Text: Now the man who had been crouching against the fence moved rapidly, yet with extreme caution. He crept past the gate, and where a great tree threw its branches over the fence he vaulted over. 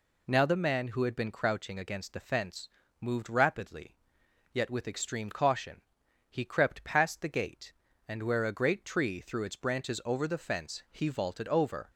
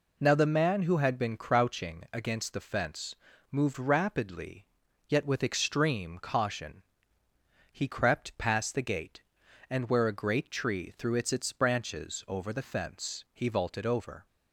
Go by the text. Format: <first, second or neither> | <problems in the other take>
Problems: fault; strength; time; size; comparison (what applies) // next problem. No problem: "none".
first | pauses between "fence" and "moved"; at 3.1 s; 0.38 s long; slight in the first // says "its" twice; at 11.3 s